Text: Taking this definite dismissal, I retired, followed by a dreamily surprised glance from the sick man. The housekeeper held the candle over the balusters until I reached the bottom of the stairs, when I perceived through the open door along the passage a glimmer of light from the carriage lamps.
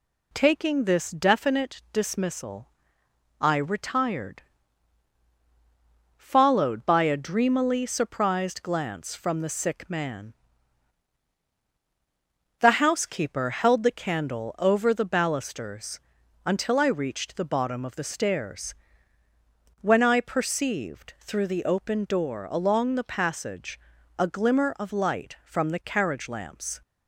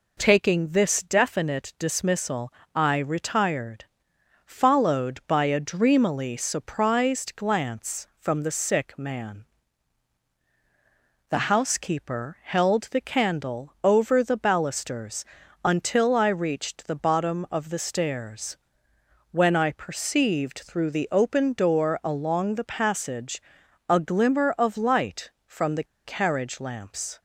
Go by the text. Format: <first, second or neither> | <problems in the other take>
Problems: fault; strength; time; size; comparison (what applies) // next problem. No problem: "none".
first | pauses between "balusters" and "until"; at 15.2 s; 0.40 s long; noticeable in the first // pauses between "passage" and "a"; noticeable; at 23.4 s; 0.48 s long; also in the first // pauses between "the" and "carriage"; slight; at 25.8 s; 0.20 s long